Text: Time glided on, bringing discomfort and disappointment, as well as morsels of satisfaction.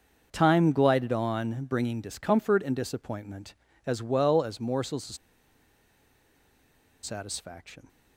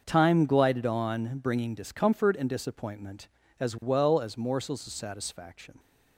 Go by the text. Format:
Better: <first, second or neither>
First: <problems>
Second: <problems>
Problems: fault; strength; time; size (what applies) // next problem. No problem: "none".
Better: second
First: starts louder than the rest; until 1.3 s; 6.5 dB // pauses between "of" and "satisfaction"; strong; at 5.1 s; 1.8 s long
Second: starts louder than the rest; until 1.0 s; 6.5 dB